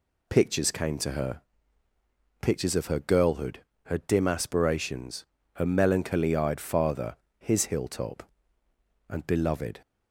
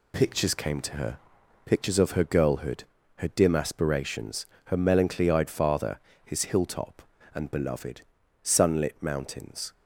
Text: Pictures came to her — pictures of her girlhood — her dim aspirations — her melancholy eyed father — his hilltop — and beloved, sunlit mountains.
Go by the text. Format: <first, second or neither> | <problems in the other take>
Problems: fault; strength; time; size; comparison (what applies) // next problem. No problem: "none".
second | stops before "sunlit mountains"; at 9.8 s